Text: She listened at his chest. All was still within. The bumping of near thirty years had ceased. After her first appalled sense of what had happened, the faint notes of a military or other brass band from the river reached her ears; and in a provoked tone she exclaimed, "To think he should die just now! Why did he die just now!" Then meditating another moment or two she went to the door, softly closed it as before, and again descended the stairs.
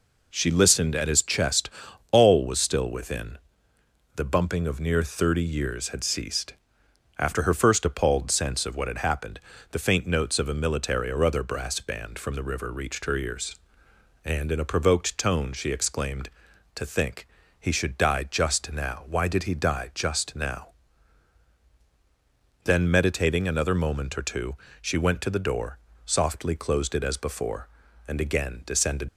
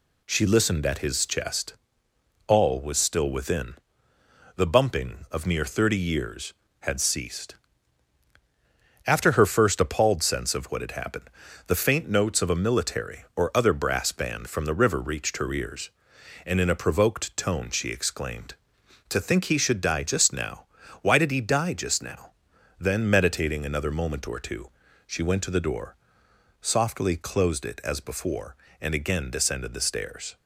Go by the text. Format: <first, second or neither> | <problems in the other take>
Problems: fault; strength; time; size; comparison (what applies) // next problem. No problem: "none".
second | pauses between "think" and "he"; slight; at 17.2 s; 0.32 s long // pauses between "two" and "she"; slight; at 24.5 s; 0.24 s long; slight in the second // stops before "the stairs"; at 29.0 s